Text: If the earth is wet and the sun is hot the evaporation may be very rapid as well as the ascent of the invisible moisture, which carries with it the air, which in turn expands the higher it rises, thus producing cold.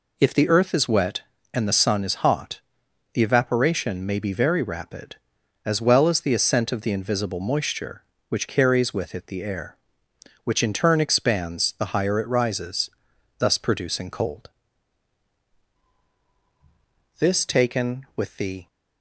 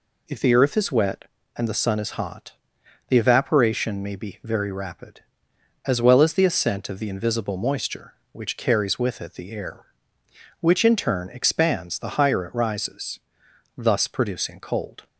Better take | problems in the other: second | pauses between "hot" and "the"; noticeable; at 2.6 s; 0.52 s long; noticeable in the second // goes on to say "This taken with the"; from 17.1 s on; 1.4 s long

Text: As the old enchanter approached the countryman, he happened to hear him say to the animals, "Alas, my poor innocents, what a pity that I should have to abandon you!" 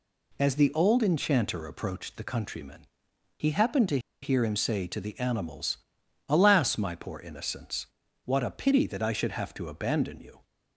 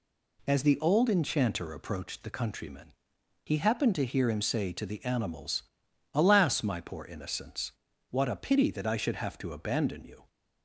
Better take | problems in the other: second | pauses between "to" and "hear"; slight; at 3.9 s; 0.23 s long

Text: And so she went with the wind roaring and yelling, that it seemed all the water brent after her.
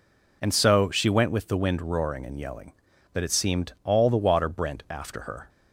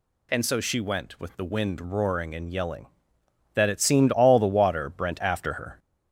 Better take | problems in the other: first | gets louder; slight; throughout; 3 dB

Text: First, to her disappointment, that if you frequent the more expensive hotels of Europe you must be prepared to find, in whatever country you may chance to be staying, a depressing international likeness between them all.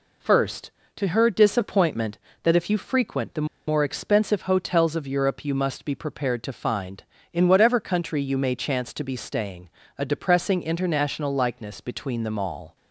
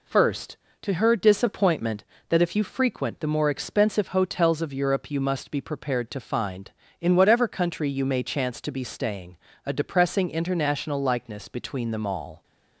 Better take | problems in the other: second | pauses between "the" and "more"; slight; at 3.4 s; 0.20 s long

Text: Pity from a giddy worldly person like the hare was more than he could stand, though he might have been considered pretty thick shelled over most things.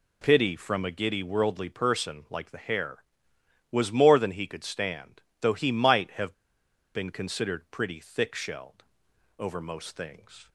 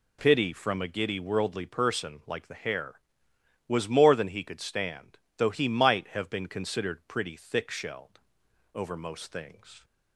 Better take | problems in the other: second | pauses between "have" and "been"; noticeable; at 6.3 s; 0.62 s long // pauses between "shelled" and "over"; noticeable; at 8.8 s; 0.56 s long; noticeable in the second

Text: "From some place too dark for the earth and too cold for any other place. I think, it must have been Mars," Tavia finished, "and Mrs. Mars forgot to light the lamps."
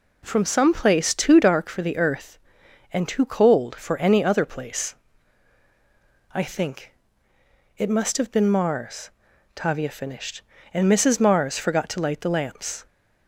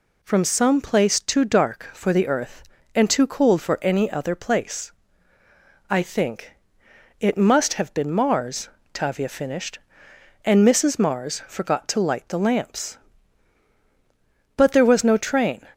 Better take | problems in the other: first | goes on to say "But there was no train"; noticeable; from 14.5 s on; 1.1 s long

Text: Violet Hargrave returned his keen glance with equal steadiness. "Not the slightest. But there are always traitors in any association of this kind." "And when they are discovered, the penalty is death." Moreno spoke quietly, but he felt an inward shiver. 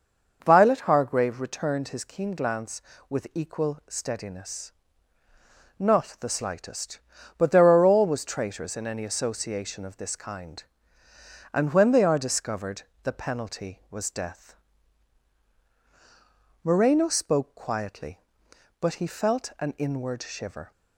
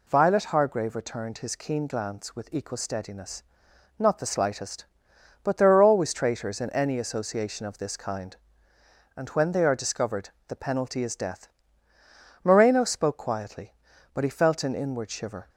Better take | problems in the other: second | says "was" for "is"; at 13.9 s

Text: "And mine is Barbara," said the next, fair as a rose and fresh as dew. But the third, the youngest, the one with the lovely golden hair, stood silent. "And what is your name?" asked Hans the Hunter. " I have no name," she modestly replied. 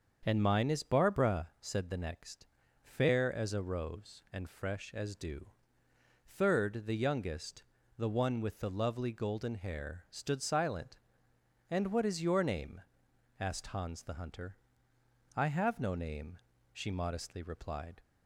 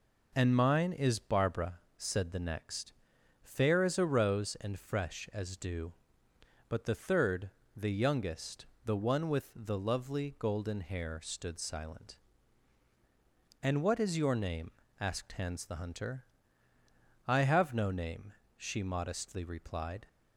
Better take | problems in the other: second | starts louder than the rest; until 1.2 s; 7 dB // skips "But the"; at 5.8 s

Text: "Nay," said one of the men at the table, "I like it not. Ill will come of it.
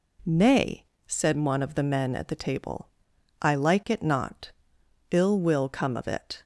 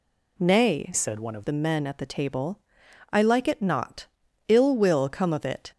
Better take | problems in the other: first | changes voice from "said" to "of"; from 0.9 to 1.4 s; 0.5 s long

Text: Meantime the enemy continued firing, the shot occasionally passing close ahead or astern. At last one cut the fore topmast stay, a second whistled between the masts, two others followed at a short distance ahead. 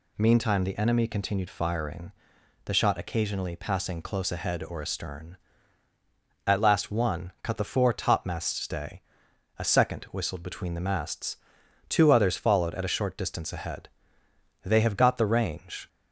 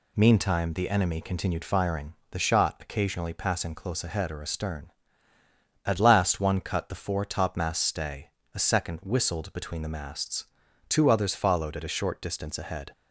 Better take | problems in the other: second | goes on to say "They have got the range"; noticeable; from 14.6 s on; 1.2 s long

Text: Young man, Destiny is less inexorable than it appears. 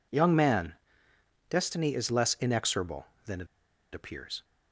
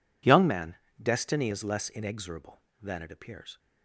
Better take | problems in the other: second | pauses between "it" and "appears"; noticeable; at 3.4 s; 0.46 s long

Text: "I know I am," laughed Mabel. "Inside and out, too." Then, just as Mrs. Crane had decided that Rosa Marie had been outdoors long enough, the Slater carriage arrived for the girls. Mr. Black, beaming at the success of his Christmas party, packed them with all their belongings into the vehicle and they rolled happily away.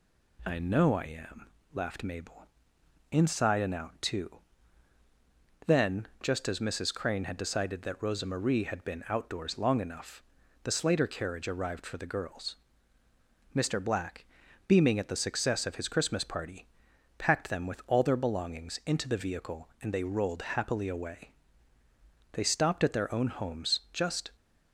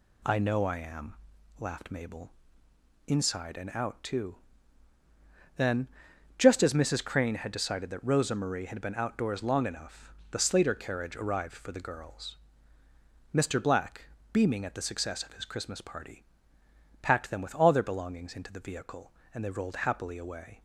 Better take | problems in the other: second | goes on to say "They stopped at their own homes just"; strong; from 22.3 s on; 1.9 s long

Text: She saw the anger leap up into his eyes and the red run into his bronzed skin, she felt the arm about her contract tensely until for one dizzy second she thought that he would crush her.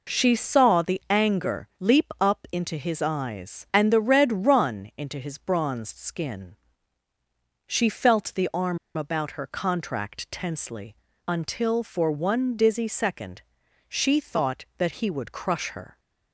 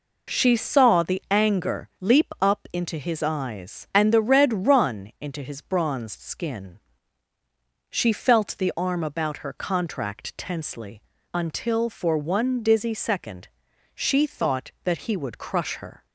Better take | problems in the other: second | pauses between "arm" and "about"; slight; at 8.7 s; 0.19 s long // pauses between "tensely" and "until"; slight; at 10.9 s; 0.32 s long; slight in the second // pauses between "second" and "she"; at 13.4 s; 0.44 s long; also in the second

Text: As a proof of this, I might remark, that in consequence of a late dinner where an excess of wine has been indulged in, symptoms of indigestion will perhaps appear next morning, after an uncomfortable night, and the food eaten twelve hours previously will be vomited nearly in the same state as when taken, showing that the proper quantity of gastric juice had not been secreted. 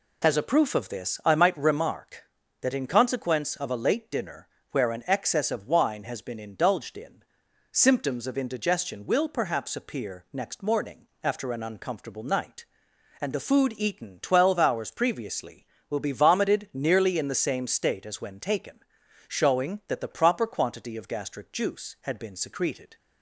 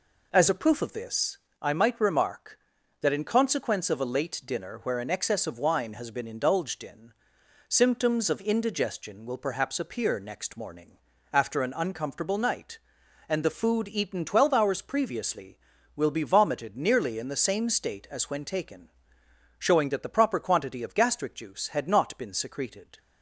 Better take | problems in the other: second | pauses between "dinner" and "where"; slight; at 4.4 s; 0.24 s long // skips "not"; at 22.1 s

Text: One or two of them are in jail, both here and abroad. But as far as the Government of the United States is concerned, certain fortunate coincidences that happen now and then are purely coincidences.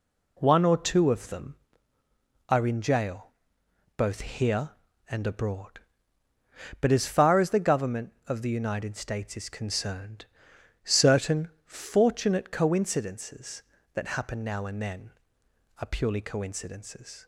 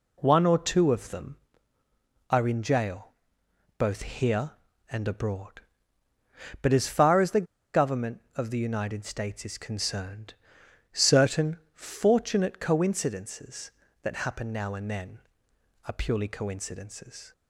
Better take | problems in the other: first | pauses between "the" and "Government"; slight; at 7.4 s; 0.27 s long // pauses between "certain" and "fortunate"; slight; at 11.5 s; 0.16 s long; slight in the first

